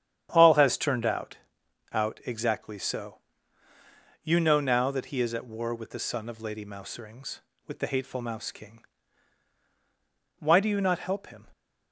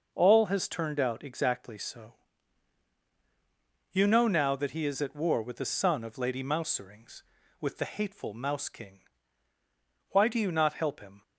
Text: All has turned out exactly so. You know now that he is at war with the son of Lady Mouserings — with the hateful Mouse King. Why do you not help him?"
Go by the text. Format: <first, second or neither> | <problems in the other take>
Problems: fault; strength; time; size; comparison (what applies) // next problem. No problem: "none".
second | starts louder than the rest; strong; until 1.3 s; 9.5 dB // says "out" twice; at 1.9 s